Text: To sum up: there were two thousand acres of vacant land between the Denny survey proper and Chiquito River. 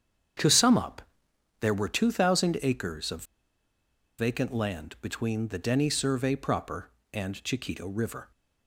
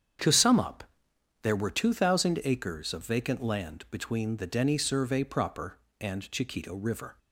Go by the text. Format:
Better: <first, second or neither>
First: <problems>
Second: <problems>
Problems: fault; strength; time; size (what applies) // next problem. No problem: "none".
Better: second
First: starts louder than the rest; strong; until 1.9 s; 8 dB // pauses between "of" and "vacant"; noticeable; at 3.2 s; 0.94 s long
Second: starts louder than the rest; strong; until 1.7 s; 8 dB